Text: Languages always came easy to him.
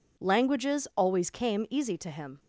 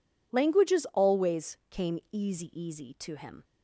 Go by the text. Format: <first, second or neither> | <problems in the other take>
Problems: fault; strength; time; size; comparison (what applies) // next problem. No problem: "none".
first | says "easy" twice; at 2.5 s